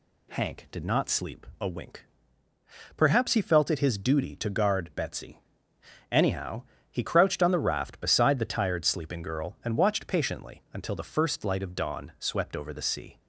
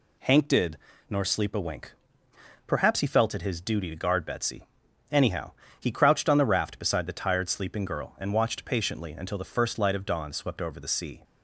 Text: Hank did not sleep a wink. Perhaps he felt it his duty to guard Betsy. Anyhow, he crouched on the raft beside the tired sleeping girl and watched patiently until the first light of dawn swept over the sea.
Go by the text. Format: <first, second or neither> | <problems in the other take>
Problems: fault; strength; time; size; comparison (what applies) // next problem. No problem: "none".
first | says "nor" for "not"; at 1.0 s